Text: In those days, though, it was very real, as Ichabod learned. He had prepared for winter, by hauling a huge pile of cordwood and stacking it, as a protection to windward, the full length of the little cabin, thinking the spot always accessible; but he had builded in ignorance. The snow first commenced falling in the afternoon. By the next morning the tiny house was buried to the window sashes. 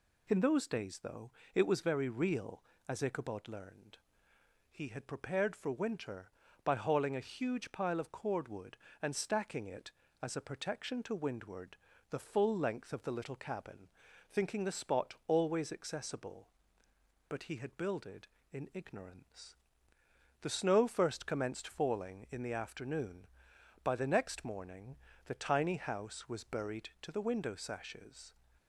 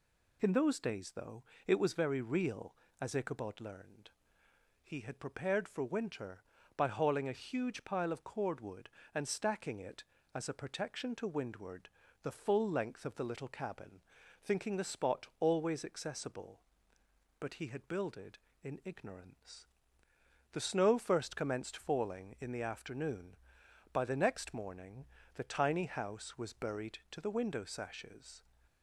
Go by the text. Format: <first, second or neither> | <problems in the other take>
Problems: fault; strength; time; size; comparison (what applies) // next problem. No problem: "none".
neither | pauses between "morning" and "the"; slight; the same in both